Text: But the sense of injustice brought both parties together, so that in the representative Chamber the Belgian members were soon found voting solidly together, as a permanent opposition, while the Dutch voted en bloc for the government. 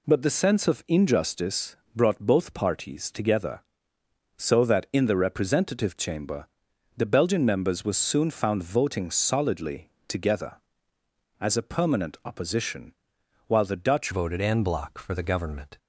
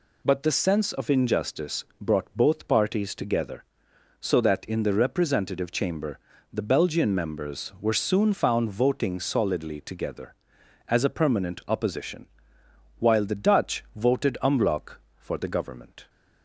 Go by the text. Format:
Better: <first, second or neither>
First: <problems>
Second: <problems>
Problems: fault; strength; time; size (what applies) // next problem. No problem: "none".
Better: second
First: pauses between "injustice" and "brought"; slight; at 1.7 s; 0.18 s long // pauses between "Chamber" and "the"; noticeable; at 6.4 s; 0.50 s long // pauses between "solidly" and "together"; slight; at 9.9 s; 0.18 s long // changes voice at "voted"; from 14.1 s on; 1.6 s long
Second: pauses between "Chamber" and "the"; slight; at 6.1 s; 0.34 s long